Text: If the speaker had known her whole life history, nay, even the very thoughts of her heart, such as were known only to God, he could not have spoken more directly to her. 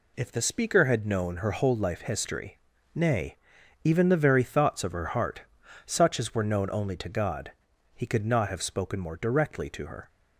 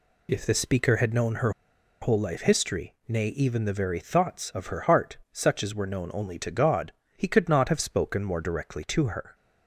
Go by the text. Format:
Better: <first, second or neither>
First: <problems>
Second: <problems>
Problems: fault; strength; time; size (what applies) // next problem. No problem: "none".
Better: first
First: none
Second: pauses between "her" and "whole"; noticeable; at 1.4 s; 0.51 s long